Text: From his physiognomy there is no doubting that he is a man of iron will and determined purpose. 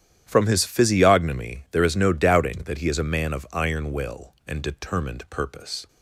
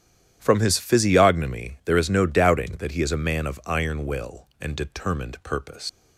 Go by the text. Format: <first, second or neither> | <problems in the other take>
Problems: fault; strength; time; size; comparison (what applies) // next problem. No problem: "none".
first | starts louder than the rest; strong; until 1.4 s; 11 dB; strong in the first // leaves "purpose" unfinished; at 5.8 s; 115 ms